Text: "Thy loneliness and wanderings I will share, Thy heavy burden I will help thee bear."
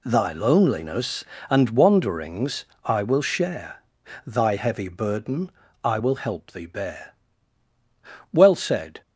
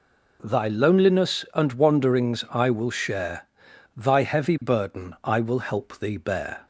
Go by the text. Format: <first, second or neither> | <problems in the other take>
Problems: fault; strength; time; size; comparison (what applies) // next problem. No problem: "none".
second | pauses between "wanderings" and "I"; slight; at 2.6 s; 0.20 s long // pauses between "burden" and "I"; slight; at 5.5 s; 0.33 s long // goes on to say "Well said"; noticeable; from 8.3 s on; 0.70 s long